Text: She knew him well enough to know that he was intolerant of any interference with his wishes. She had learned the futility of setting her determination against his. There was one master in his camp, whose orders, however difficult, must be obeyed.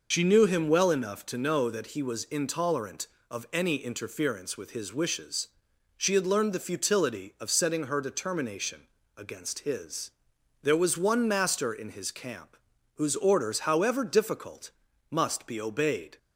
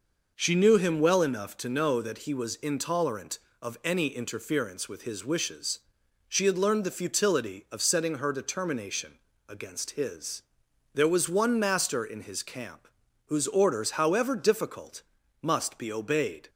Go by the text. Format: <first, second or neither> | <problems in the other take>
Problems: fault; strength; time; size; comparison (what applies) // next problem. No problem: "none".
second | loses the start of "She"; at 0.1 s; 65 ms // pauses between "determination" and "against"; slight; at 8.8 s; 0.30 s long; slight in the second